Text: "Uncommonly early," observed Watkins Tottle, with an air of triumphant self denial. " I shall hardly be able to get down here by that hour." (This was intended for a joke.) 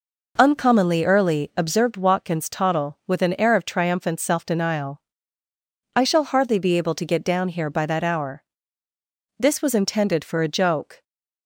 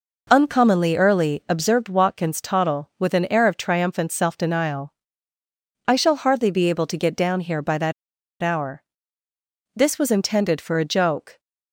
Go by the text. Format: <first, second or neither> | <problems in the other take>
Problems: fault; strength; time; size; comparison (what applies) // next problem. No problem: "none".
first | pauses between "that" and "hour"; noticeable; at 7.9 s; 0.49 s long